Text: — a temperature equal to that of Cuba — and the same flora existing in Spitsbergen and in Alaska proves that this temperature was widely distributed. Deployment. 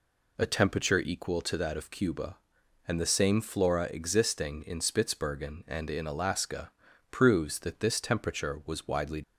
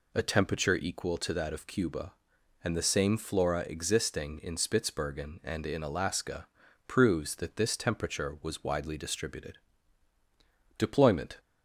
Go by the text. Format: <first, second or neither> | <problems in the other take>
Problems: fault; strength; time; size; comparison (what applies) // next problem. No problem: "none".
second | pauses between "Alaska" and "proves"; at 6.7 s; 0.40 s long; also in the second // stops before "distributed Deployment"; at 9.2 s